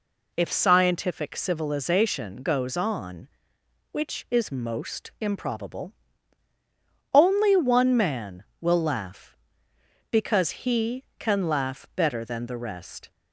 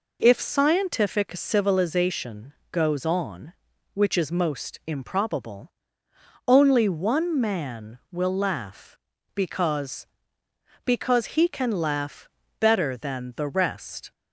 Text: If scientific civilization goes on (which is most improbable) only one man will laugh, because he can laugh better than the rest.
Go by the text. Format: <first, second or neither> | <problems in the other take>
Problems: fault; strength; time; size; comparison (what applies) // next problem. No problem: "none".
first | pauses between "civilization" and "goes"; slight; at 2.5 s; 0.18 s long // says "because" twice; at 10.8 s // pauses between "laugh" and "better"; slight; at 12.2 s; 0.30 s long